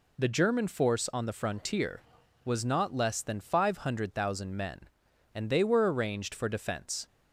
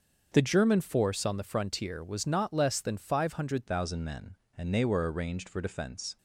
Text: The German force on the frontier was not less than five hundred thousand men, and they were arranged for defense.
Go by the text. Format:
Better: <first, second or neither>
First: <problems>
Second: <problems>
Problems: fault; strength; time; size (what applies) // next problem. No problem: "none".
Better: first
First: none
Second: starts louder than the rest; until 1.3 s; 6.5 dB // changes voice at "thousand"; from 3.6 s on; 2.5 s long